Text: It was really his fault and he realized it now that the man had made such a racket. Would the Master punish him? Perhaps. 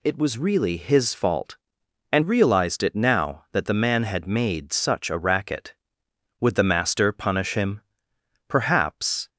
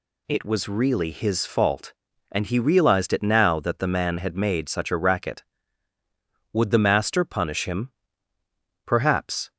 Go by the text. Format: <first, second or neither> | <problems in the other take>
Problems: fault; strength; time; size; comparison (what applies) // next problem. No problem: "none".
second | skips "he"; at 2.2 s